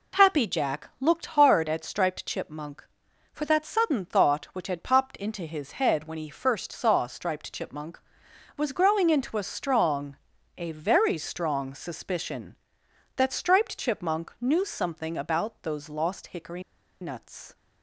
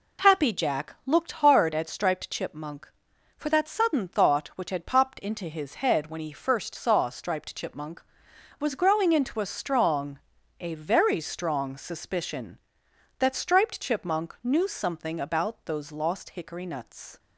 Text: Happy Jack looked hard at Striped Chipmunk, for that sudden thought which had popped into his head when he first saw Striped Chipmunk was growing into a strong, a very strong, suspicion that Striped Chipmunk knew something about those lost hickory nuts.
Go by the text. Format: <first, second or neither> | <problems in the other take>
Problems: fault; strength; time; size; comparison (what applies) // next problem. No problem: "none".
second | pauses between "hickory" and "nuts"; at 16.6 s; 0.39 s long